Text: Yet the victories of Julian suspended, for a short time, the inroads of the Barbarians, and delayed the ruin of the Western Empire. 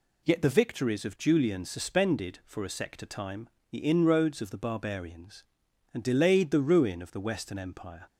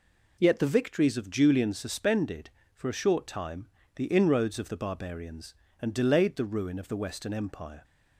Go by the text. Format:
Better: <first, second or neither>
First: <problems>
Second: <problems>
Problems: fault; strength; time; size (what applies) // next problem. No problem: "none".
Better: second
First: says "sector" for "short"; at 2.6 s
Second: none